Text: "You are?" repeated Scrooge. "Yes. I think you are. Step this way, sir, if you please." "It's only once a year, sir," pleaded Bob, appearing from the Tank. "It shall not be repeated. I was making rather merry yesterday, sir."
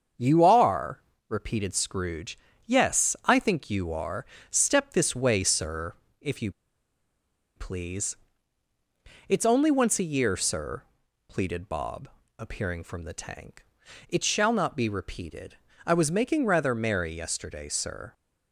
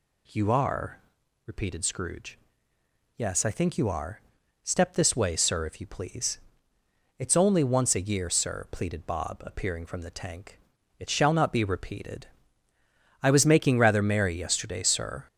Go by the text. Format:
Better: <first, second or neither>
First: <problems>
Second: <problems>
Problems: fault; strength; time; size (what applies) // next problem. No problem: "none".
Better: second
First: starts louder than the rest; until 1.4 s; 7 dB // pauses between "you" and "please"; at 6.5 s; 1.0 s long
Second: none